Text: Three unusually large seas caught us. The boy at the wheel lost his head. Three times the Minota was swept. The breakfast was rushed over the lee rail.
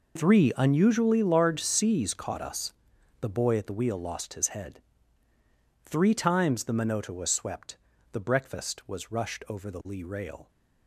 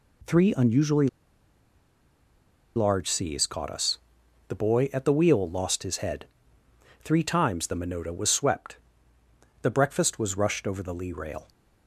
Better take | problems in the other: first | pauses between "unusually" and "large"; strong; at 1.0 s; 1.6 s long

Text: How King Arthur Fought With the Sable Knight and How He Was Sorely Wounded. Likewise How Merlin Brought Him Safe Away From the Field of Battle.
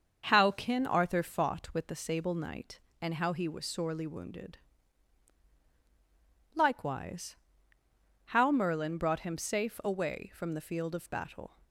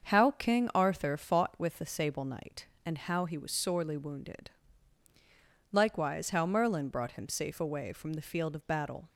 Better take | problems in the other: second | starts louder than the rest; until 1.2 s; 6.5 dB; also in the second // says "Kin" for "King"; at 0.5 s // pauses between "Likewise" and "How"; noticeable; at 7.3 s; 0.92 s long

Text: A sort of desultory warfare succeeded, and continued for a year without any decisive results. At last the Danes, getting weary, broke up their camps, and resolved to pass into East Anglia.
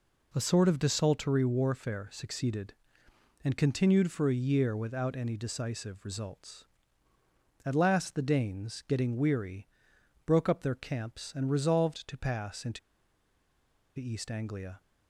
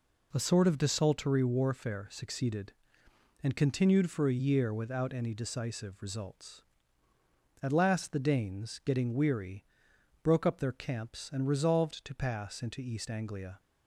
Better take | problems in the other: second | pauses between "into" and "East"; at 12.7 s; 1.1 s long

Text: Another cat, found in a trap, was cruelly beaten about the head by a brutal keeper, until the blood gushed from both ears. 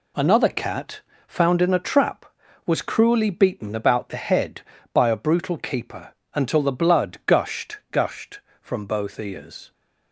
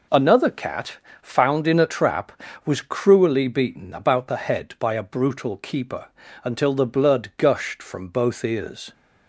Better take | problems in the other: second | says "gushed" twice; at 7.9 s

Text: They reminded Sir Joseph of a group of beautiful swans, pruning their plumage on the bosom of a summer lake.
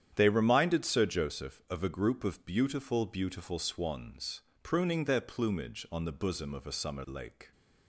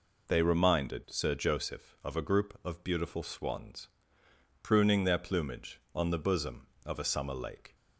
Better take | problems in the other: second | starts louder than the rest; strong; until 1.1 s; 9.5 dB // says "beautiful" twice; at 3.0 s

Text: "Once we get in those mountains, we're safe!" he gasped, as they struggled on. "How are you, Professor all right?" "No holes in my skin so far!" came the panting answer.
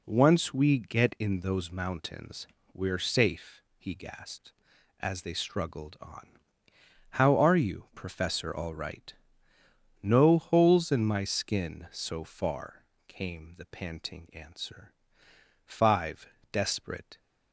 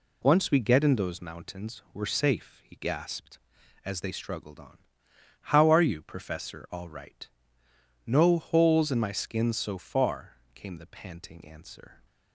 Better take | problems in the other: second | goes on to say "Five desperate"; from 15.6 s on; 1.5 s long

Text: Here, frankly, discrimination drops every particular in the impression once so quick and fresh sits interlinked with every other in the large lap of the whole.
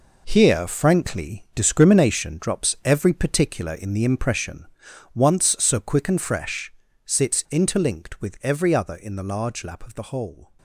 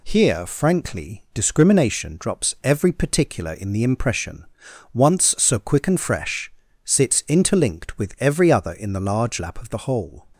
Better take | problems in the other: second | gets quieter; strong; throughout; 10.5 dB // pauses between "impression" and "once"; noticeable; at 4.6 s; 0.48 s long; noticeable in the second // pauses between "fresh" and "sits"; slight; at 6.7 s; 0.32 s long; slight in the second

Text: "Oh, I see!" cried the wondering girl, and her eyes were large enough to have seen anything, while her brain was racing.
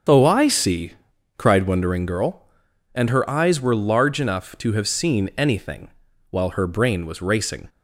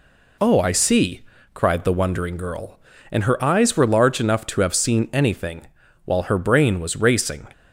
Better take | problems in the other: second | starts louder than the rest; until 1.5 s; 6.5 dB // skips "the"; at 1.6 s

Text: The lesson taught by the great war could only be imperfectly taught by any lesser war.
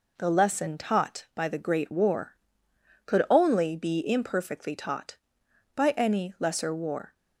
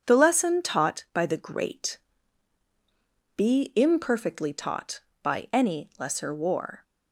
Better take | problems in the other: first | skips "war could only"; at 2.6 s

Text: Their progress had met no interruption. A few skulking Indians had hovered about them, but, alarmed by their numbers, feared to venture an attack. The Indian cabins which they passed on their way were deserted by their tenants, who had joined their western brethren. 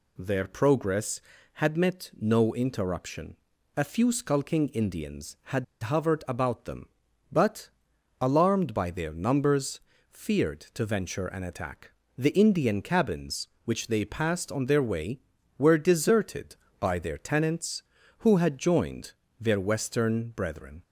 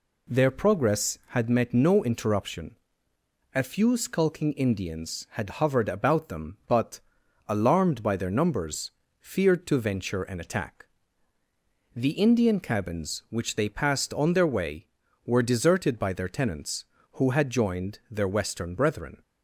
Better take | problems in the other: second | pauses between "had" and "hovered"; slight; at 5.6 s; 0.19 s long // pauses between "joined" and "their"; slight; at 19.1 s; 0.28 s long

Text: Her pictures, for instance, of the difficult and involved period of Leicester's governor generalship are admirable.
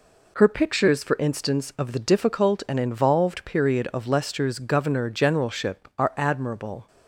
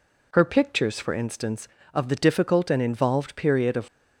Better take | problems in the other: first | stops before "Leicester's governor generalship are admirable"; at 3.8 s

